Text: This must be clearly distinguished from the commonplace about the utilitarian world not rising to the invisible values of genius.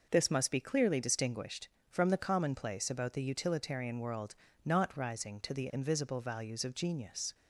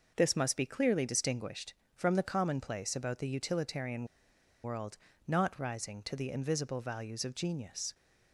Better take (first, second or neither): first